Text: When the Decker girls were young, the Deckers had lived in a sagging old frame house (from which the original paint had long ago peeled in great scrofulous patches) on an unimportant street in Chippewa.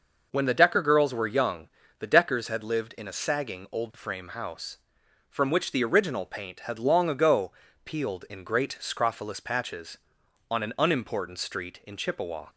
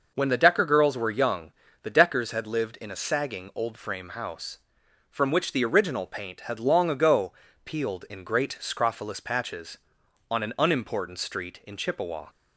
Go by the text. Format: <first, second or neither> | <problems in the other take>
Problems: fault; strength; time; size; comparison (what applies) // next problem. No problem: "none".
neither | pauses between "ago" and "peeled"; slight; the same in both